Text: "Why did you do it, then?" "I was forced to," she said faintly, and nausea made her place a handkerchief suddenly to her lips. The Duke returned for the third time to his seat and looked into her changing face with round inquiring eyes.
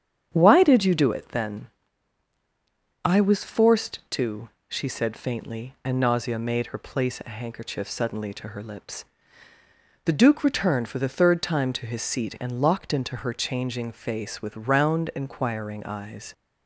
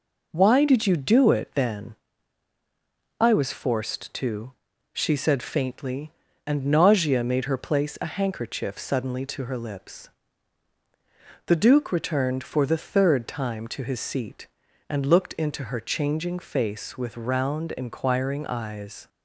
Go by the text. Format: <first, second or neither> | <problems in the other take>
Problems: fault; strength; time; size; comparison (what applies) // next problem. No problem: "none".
second | starts louder than the rest; strong; until 1.3 s; 8.5 dB // says "locked" for "looked"; at 12.6 s